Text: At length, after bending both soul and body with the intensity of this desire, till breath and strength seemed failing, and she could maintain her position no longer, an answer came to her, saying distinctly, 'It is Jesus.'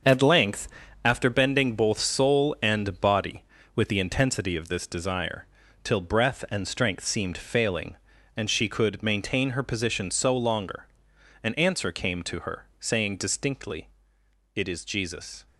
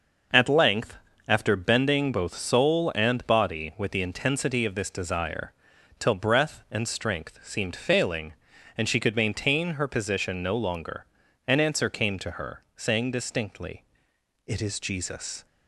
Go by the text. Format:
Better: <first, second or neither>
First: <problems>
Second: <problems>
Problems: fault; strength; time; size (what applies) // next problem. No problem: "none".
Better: second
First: starts louder than the rest; until 1.4 s; 6.5 dB // says "so" for "no"; at 10.0 s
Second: none